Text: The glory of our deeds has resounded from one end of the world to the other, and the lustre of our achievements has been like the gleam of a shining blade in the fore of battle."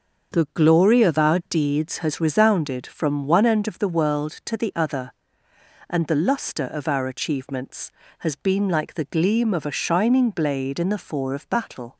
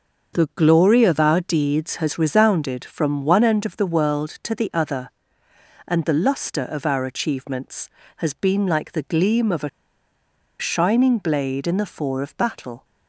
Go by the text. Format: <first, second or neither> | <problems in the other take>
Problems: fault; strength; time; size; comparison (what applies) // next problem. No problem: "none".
first | starts louder than the rest; until 1.4 s; 6.5 dB; also in the first // pauses between "a" and "shining"; noticeable; at 9.6 s; 0.91 s long